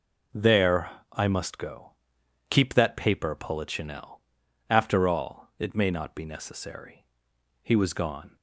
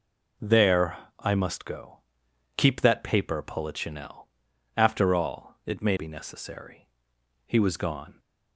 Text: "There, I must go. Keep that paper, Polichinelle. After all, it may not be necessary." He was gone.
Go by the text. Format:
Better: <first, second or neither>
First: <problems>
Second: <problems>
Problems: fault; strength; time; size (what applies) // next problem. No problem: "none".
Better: first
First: none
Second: skips "not"; at 5.9 s